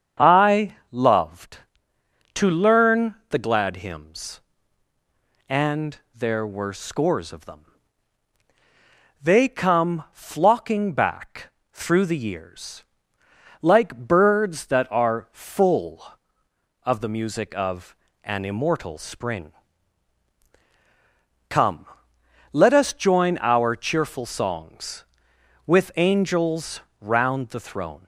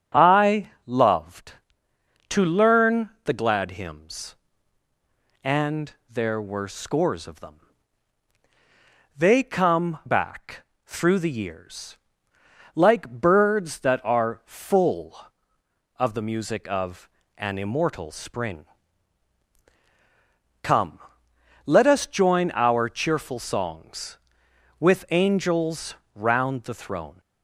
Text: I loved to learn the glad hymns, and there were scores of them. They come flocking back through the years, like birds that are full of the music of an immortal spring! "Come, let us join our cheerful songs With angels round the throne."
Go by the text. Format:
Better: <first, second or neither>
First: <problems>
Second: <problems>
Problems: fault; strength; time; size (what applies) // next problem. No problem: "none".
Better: first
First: starts louder than the rest; strong; until 1.3 s; 7.5 dB // pauses between "I" and "loved"; slight; at 0.7 s; 0.16 s long // pauses between "and" and "there"; slight; at 5.9 s; 0.16 s long // pauses between "back" and "through"; slight; at 11.5 s; 0.22 s long // pauses between "of" and "an"; slight; at 17.9 s; 0.30 s long // pauses between "angels" and "round"; slight; at 26.7 s; 0.20 s long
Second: starts louder than the rest; strong; until 1.3 s; 7.5 dB // pauses between "I" and "loved"; slight; at 0.6 s; 0.16 s long // pauses between "and" and "there"; slight; at 5.9 s; 0.16 s long // skips "flocking"; at 10.0 s // pauses between "back" and "through"; slight; at 10.6 s; 0.22 s long // pauses between "of" and "an"; slight; at 17.0 s; 0.30 s long // pauses between "angels" and "round"; slight; at 25.9 s; 0.20 s long